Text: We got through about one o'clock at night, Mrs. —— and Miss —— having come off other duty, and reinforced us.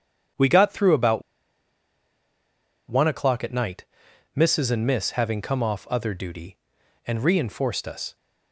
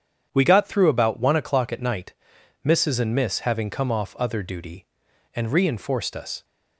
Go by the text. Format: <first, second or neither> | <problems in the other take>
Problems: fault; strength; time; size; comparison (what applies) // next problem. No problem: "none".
second | starts louder than the rest; strong; until 3.0 s; 8.5 dB; strong in the second // pauses between "about" and "one"; strong; at 1.2 s; 1.6 s long